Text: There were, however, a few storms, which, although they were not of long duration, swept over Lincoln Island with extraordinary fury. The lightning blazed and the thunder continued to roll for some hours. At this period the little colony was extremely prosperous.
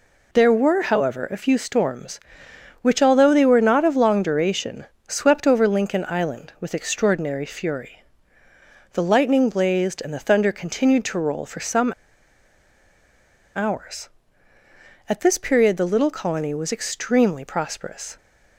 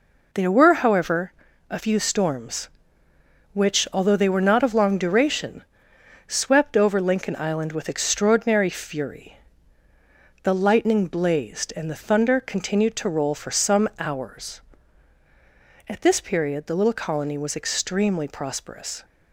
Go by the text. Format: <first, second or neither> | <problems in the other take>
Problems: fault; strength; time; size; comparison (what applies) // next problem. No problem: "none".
second | pauses between "some" and "hours"; strong; at 11.9 s; 1.6 s long